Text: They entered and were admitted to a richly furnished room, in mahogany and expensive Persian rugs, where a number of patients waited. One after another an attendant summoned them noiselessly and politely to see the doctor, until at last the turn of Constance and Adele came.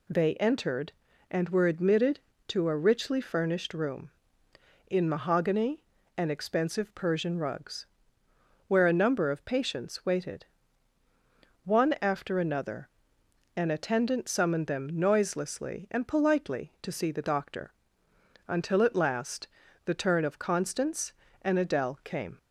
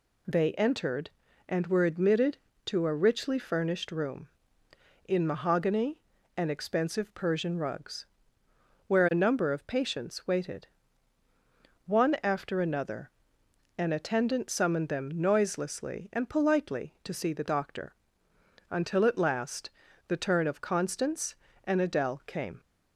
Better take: neither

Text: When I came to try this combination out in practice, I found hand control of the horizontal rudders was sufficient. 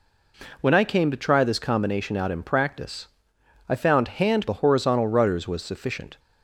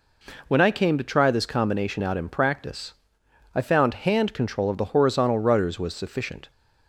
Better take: second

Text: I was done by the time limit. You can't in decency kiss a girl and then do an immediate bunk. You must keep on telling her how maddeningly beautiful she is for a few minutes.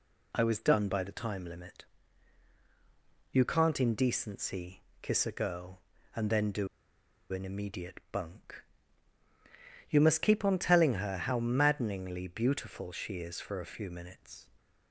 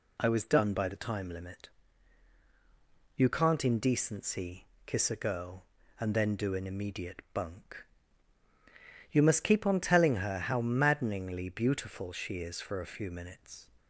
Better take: second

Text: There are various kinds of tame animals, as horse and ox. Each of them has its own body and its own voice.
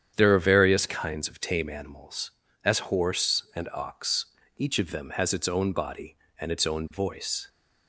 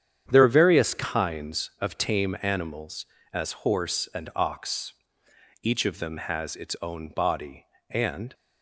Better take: first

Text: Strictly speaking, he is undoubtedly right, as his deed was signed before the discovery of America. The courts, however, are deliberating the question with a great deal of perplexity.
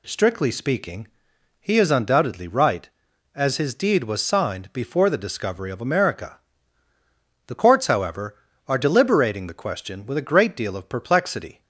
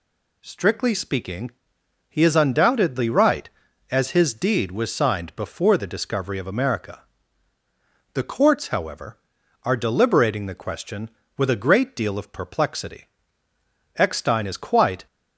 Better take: first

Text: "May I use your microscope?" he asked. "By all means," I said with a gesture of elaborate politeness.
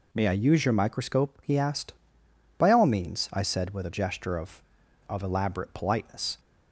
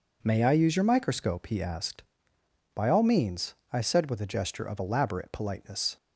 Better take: second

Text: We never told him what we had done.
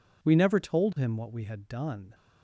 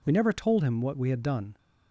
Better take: neither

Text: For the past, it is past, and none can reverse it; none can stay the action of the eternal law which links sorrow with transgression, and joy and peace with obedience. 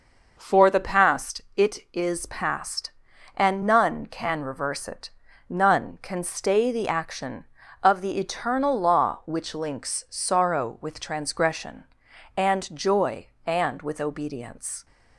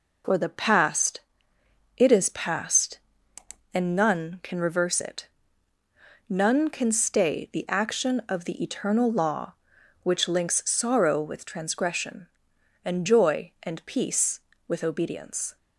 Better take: second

